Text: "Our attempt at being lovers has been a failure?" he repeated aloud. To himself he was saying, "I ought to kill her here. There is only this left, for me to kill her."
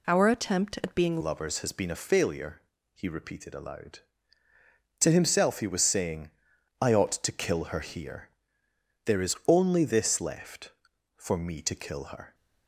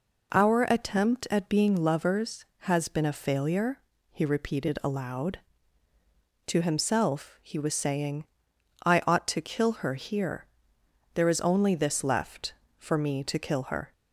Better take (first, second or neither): second